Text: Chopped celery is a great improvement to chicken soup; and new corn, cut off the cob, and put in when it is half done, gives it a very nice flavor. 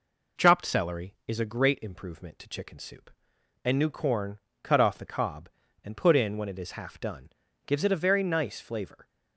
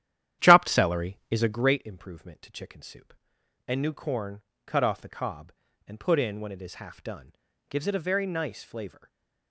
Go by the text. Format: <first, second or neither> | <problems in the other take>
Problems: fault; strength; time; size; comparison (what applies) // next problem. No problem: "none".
first | starts louder than the rest; strong; until 1.9 s; 11 dB // stays silent after the last word; slight; from 8.9 s on; 0.6 s long